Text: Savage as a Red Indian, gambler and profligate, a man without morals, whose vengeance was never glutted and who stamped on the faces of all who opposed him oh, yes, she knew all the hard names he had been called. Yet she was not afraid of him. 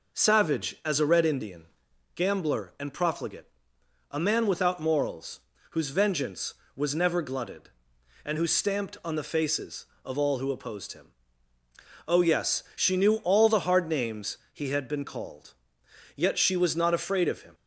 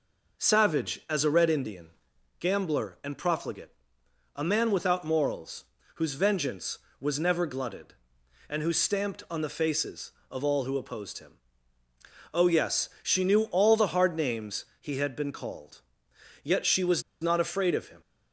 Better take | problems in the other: first | pauses between "him" and "oh"; at 11.3 s; 1.0 s long; also in the first // pauses between "was" and "not"; slight; at 17.0 s; 0.19 s long

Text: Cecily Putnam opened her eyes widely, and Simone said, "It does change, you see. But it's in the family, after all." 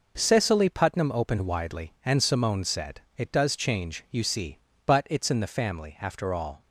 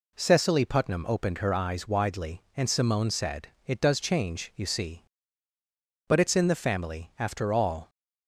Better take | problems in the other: second | skips "her eyes"; at 1.4 s

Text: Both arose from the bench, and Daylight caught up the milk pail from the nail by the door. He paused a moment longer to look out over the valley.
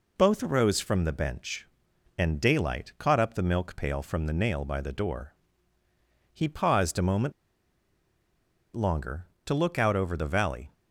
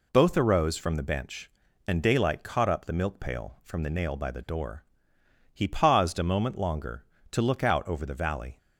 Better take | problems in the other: second | pauses between "moment" and "longer"; strong; at 7.3 s; 1.4 s long

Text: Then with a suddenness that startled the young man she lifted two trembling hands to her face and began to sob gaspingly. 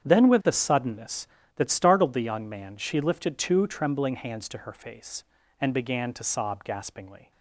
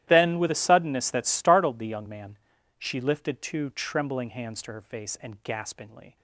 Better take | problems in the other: first | starts louder than the rest; strong; until 1.0 s; 13 dB; strong in the first // pauses between "man" and "she"; at 2.3 s; 0.40 s long // skips "began to sob"; at 5.4 s

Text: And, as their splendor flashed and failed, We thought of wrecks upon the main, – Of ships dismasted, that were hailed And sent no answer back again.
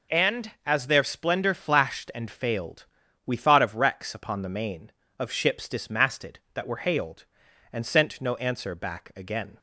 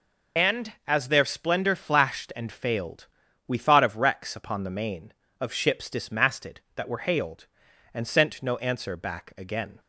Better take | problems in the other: first | loses the start of "And"; at 0.3 s; 40 ms

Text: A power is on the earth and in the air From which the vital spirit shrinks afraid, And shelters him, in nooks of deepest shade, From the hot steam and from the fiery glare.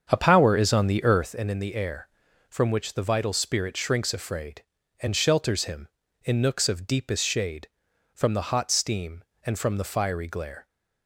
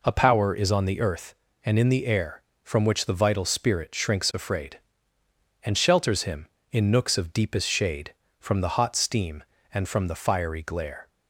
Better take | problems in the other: second | starts louder than the rest; strong; until 1.5 s; 7.5 dB

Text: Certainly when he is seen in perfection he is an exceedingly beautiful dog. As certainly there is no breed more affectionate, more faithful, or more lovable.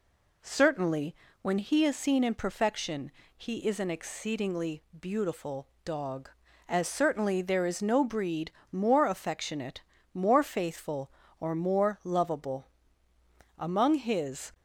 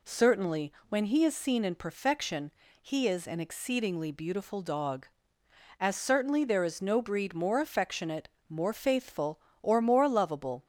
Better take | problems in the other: second | pauses between "Certainly" and "when"; slight; at 1.1 s; 0.26 s long; slight in the second // pauses between "perfection" and "he"; slight; at 3.1 s; 0.24 s long; slight in the second // pauses between "exceedingly" and "beautiful"; slight; at 4.8 s; 0.16 s long // pauses between "beautiful" and "dog"; slight; at 5.6 s; 0.16 s long // pauses between "breed" and "more"; slight; at 8.4 s; 0.22 s long // goes on to say "Among his"; noticeable; from 13.5 s on; 0.96 s long

